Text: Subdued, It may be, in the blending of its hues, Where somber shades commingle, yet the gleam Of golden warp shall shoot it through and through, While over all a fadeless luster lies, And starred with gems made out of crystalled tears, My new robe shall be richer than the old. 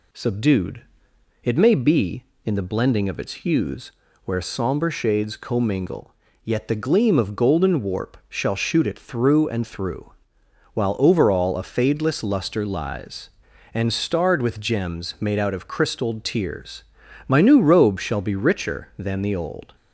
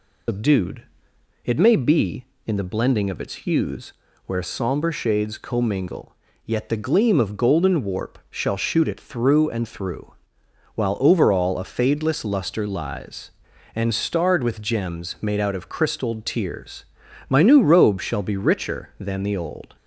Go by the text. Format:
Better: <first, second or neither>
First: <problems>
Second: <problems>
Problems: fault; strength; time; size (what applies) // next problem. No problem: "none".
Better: first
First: none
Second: loses the start of "Subdued"; at 0.2 s; 140 ms